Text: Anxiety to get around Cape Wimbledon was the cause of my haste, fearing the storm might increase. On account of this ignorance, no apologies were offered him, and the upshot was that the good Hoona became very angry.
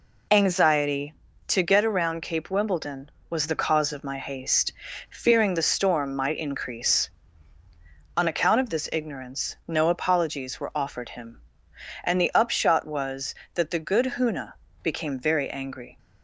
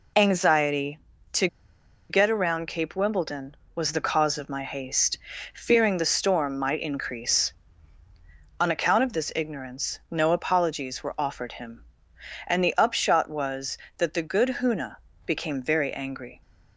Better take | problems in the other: first | pauses between "to" and "get"; noticeable; at 1.4 s; 0.63 s long // pauses between "Hoona" and "became"; slight; at 14.9 s; 0.30 s long; slight in the first

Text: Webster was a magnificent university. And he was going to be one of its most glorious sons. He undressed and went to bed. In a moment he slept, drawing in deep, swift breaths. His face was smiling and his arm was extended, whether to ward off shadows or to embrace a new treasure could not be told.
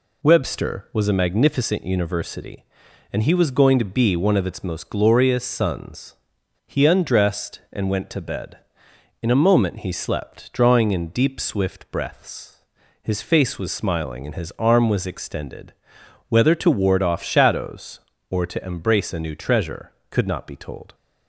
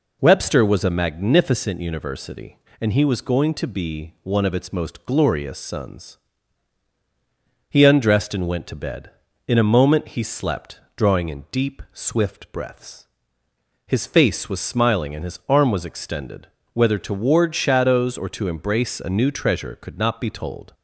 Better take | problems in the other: first | skips "off"; at 17.5 s

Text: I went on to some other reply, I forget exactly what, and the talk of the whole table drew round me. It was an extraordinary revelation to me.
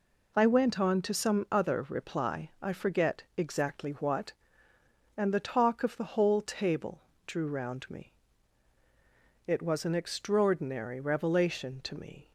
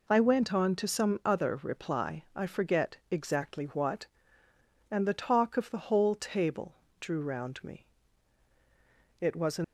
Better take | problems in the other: first | pauses between "forget" and "exactly"; slight; at 2.9 s; 0.16 s long; slight in the first // pauses between "table" and "drew"; slight; at 6.7 s; 0.26 s long; slight in the first // stops before "extraordinary revelation to me"; at 9.6 s

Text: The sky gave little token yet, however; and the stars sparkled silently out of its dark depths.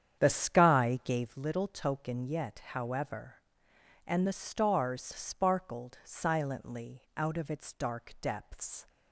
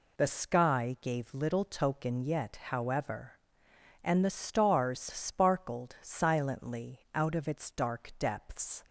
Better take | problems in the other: second | starts louder than the rest; strong; until 1.4 s; 8.5 dB // pauses between "silently" and "out"; slight; at 7.0 s; 0.16 s long; slight in the second

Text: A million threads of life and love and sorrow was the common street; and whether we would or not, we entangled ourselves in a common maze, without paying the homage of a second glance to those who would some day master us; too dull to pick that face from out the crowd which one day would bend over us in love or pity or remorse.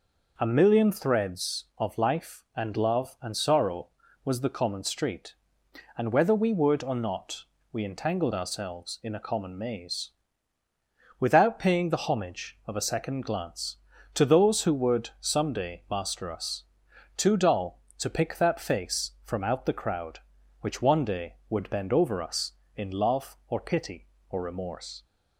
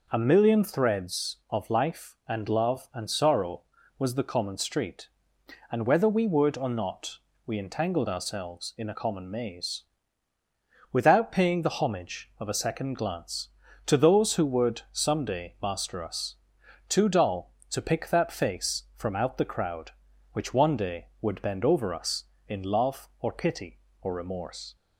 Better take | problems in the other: neither | none

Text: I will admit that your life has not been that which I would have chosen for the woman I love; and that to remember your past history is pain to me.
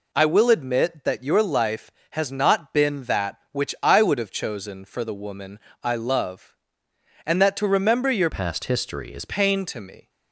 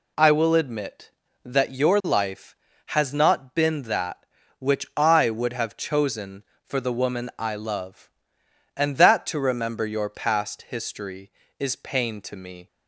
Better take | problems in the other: second | pauses between "woman" and "I"; slight; at 5.5 s; 0.24 s long // changes voice from "past" to "is"; from 8.2 to 9.2 s; 1.0 s long

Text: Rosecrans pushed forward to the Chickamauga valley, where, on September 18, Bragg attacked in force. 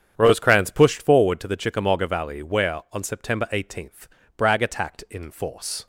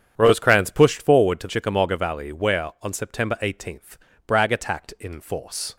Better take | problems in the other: first | starts louder than the rest; strong; until 1.1 s; 8.5 dB; strong in the first // skips "the"; at 1.4 s

